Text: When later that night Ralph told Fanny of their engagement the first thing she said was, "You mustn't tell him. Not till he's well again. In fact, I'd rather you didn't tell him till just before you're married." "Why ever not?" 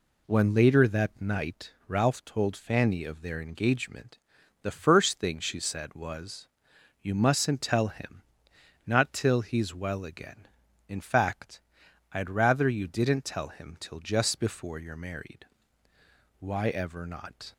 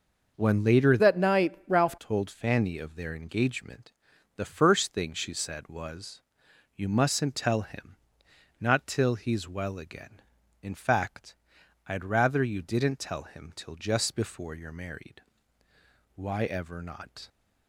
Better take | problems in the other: first | starts louder than the rest; until 1.4 s; 6 dB // changes voice from "that" to "Ralph"; from 0.9 to 1.9 s; 1.0 s long // pauses between "engagement" and "the"; noticeable; at 3.9 s; 0.46 s long; noticeable in the first

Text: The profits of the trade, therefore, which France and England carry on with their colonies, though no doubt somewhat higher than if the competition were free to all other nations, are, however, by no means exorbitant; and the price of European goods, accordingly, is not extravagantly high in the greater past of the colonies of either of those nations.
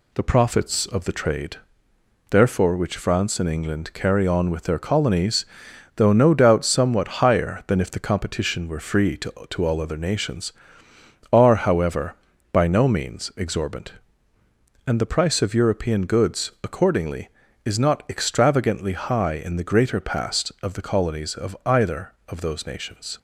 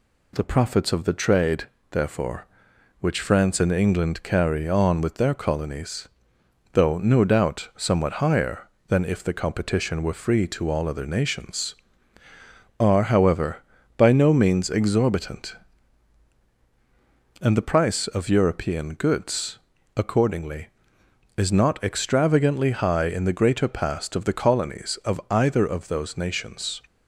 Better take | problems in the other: second | says "to" twice; at 9.4 s

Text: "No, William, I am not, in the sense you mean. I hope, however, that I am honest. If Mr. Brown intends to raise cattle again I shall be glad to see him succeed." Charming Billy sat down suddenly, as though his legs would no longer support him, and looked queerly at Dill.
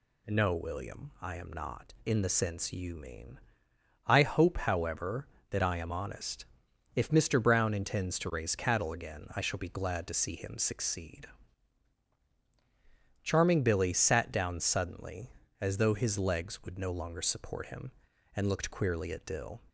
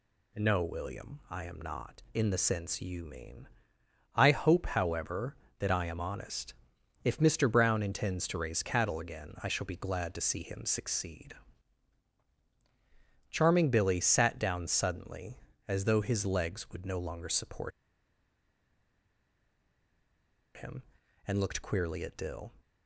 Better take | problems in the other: first | pauses between "support" and "him"; strong; at 17.7 s; 2.8 s long

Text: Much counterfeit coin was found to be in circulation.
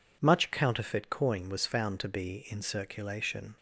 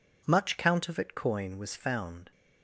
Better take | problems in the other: first | stops before "to be in circulation"; at 2.3 s

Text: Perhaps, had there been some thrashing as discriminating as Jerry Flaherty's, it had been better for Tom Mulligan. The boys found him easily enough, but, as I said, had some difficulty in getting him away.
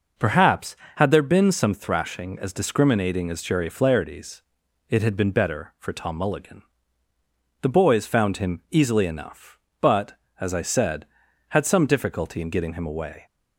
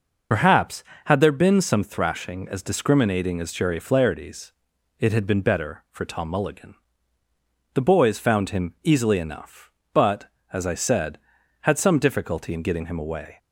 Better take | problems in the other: first | loses the start of "Perhaps"; at 0.3 s; 50 ms

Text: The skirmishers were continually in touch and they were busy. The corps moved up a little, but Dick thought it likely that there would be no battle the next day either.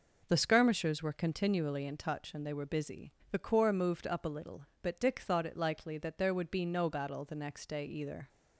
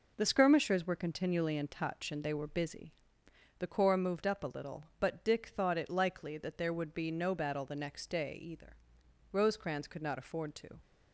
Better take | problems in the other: first | goes on to say "Rosecrans could not afford to"; from 9.3 s on; 1.4 s long

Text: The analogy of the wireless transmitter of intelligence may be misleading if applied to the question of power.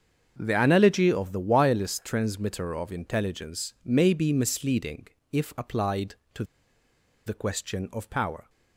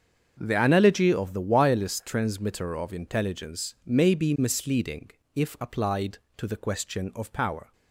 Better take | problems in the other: second | starts louder than the rest; until 1.3 s; 6.5 dB; also in the second // pauses between "misleading" and "if"; slight; at 5.0 s; 0.26 s long; slight in the second // pauses between "to" and "the"; noticeable; at 6.4 s; 0.83 s long

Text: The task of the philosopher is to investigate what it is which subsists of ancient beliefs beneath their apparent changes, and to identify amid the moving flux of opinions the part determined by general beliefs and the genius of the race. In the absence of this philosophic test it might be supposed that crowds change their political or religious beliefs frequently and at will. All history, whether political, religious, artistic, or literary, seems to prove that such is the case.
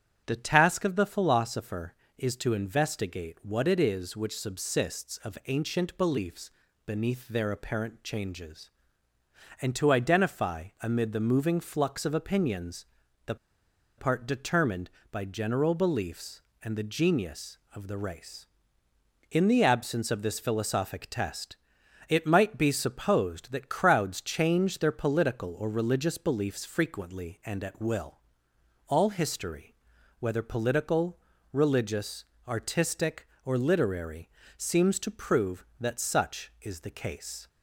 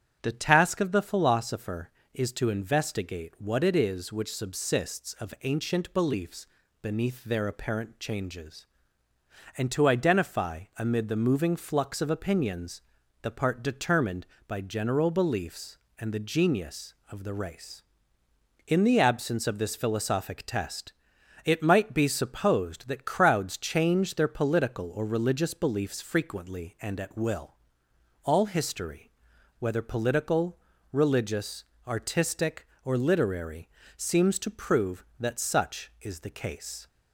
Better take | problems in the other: second | starts louder than the rest; strong; until 1.2 s; 8.5 dB; strong in the second // pauses between "beliefs" and "beneath"; slight; at 6.4 s; 0.36 s long; slight in the second // pauses between "opinions" and "the"; at 12.8 s; 0.40 s long; also in the second // pauses between "the" and "part"; noticeable; at 13.3 s; 0.62 s long // pauses between "test" and "it"; noticeable; at 21.5 s; 0.54 s long; noticeable in the second

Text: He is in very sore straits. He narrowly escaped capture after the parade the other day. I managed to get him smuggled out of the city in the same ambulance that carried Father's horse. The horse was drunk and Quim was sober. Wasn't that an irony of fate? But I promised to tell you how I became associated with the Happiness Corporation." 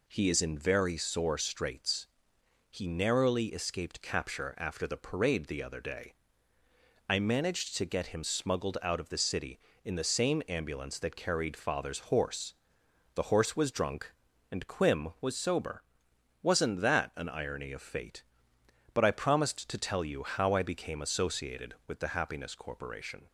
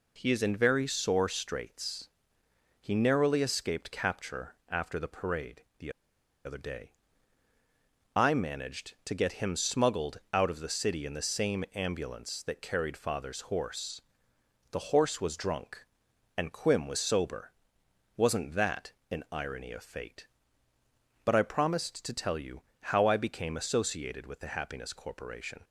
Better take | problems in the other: first | pauses between "parade" and "the"; slight; at 5.6 s; 0.16 s long // pauses between "the" and "other"; noticeable; at 5.9 s; 0.54 s long // pauses between "that" and "an"; slight; at 18.9 s; 0.18 s long // pauses between "you" and "how"; slight; at 22.6 s; 0.18 s long

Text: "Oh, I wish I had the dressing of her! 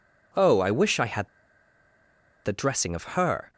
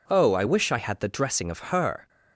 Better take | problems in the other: second | pauses between "had" and "the"; at 1.2 s; 1.1 s long

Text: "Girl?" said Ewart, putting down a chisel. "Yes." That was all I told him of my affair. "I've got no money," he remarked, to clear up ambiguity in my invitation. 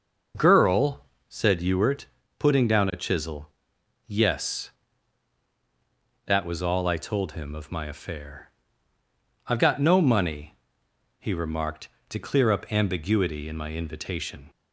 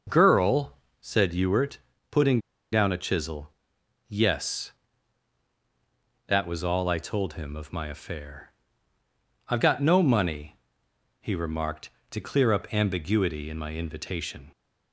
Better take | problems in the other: first | pauses between "putting" and "down"; slight; at 2.3 s; 0.32 s long

